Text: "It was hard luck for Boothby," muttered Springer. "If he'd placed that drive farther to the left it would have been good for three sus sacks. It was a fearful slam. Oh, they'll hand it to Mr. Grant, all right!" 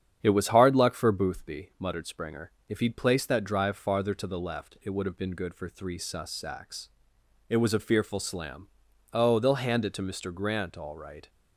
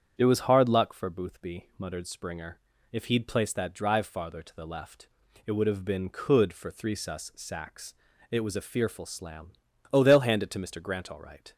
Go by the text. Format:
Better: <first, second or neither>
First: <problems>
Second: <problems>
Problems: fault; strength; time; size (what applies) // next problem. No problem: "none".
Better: first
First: starts louder than the rest; strong; until 1.2 s; 8.5 dB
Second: starts louder than the rest; strong; until 1.1 s; 8 dB // pauses between "left" and "it"; at 5.0 s; 0.40 s long // says "could" for "good"; at 6.0 s